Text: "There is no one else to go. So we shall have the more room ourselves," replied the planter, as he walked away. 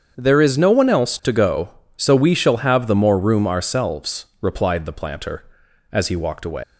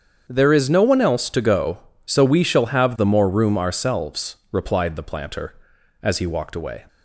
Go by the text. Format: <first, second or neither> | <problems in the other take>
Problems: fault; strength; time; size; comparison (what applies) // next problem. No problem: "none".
second | starts louder than the rest; strong; until 1.1 s; 7.5 dB; strong in the second // leaves "away" unfinished; at 6.6 s; 130 ms